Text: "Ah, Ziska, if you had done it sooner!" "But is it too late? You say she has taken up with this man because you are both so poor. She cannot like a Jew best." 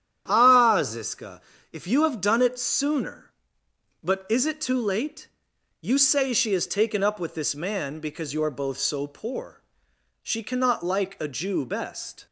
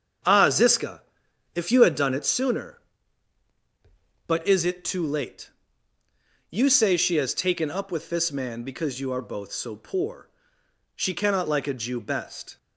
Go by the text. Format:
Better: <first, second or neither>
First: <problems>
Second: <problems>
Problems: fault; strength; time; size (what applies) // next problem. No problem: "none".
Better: second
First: starts louder than the rest; strong; until 1.2 s; 10 dB // says "have" for "had"; at 2.0 s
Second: starts louder than the rest; strong; until 1.7 s; 7.5 dB